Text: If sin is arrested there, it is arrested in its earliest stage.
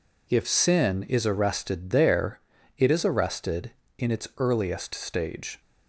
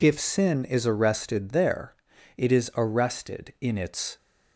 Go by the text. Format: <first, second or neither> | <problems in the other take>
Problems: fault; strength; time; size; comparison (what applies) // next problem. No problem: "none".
first | stops before "earliest stage"; at 4.1 s